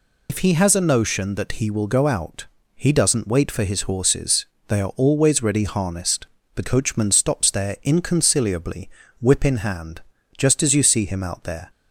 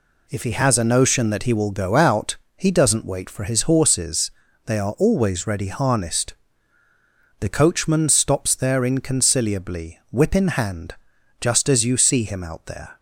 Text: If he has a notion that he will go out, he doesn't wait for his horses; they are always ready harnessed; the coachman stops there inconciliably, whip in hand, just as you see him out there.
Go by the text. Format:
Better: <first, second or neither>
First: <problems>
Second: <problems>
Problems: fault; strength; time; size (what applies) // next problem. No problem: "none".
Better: second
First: loses the start of "If"; at 0.2 s; 60 ms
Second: none